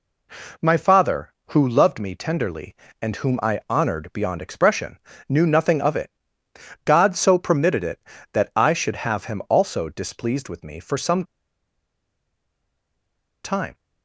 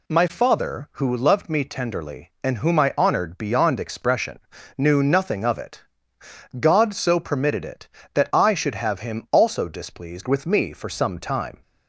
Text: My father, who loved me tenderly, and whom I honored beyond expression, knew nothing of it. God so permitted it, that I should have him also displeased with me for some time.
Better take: second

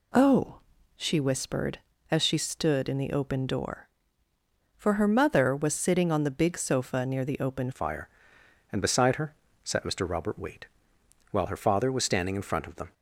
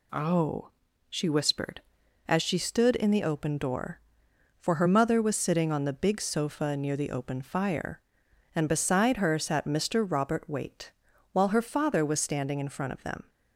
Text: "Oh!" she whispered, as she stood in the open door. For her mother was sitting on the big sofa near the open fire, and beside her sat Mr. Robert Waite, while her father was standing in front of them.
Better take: second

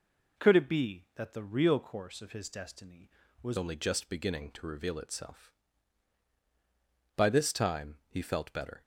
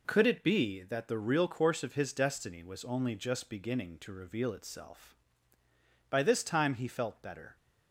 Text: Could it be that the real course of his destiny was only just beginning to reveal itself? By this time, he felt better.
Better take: second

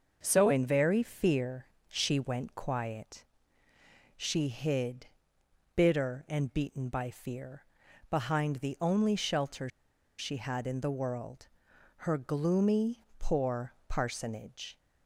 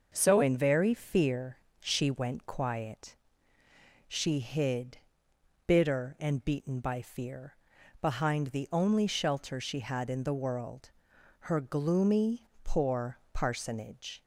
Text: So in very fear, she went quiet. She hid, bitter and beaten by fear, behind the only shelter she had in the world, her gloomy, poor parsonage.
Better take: second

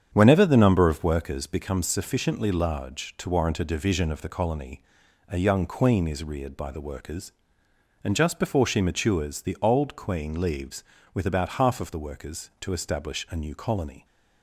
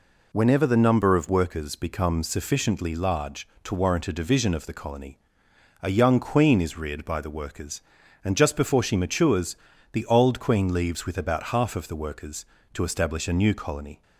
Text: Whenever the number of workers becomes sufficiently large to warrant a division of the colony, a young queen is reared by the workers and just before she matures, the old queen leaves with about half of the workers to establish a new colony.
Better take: second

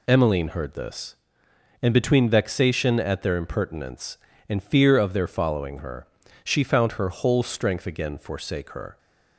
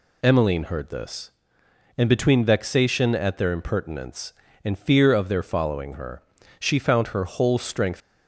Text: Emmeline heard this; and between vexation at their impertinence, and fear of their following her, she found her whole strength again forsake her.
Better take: first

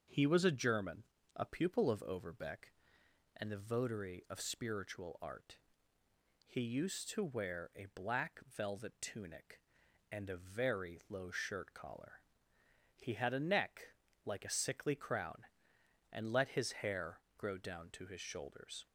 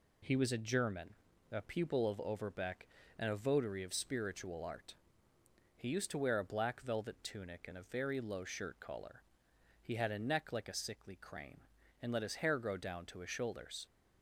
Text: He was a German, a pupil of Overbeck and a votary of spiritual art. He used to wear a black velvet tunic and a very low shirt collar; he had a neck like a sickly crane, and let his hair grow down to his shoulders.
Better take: second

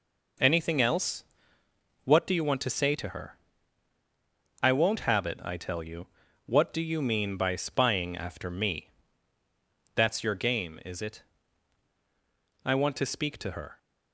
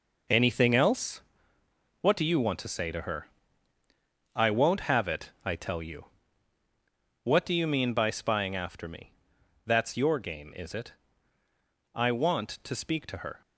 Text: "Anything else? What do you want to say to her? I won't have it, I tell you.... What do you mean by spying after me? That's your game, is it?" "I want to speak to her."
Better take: first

